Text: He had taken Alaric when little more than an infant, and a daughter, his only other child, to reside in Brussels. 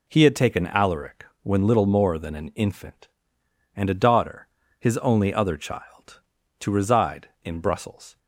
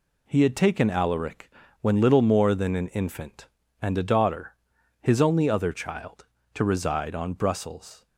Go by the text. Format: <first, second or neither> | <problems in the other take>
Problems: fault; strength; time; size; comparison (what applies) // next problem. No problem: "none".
first | pauses between "Alaric" and "when"; slight; at 1.4 s; 0.32 s long; slight in the first // says "on" for "in"; at 7.1 s